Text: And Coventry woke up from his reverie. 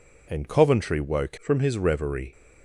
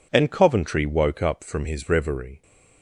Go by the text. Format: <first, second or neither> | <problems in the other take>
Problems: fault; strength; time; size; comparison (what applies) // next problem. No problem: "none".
second | skips "up"; at 1.3 s